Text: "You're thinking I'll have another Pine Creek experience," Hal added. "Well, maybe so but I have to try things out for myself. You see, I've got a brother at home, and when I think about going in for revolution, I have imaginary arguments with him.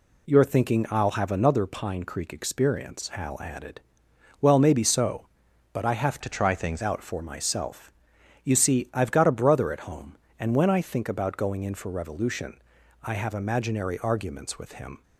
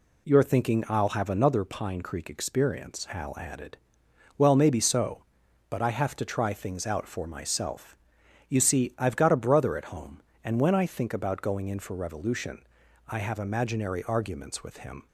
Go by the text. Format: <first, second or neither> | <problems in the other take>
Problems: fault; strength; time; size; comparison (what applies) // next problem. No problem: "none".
second | changes voice from "to" to "things"; from 6.2 to 6.8 s; 0.6 s long